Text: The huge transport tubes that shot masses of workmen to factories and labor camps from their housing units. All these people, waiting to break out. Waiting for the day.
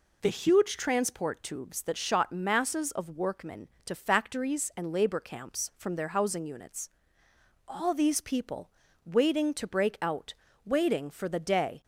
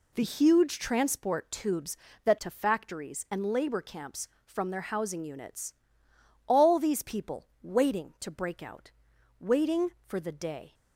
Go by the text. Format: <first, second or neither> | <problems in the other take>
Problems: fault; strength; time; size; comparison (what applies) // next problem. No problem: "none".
first | skips "shot masses of workmen"; at 2.3 s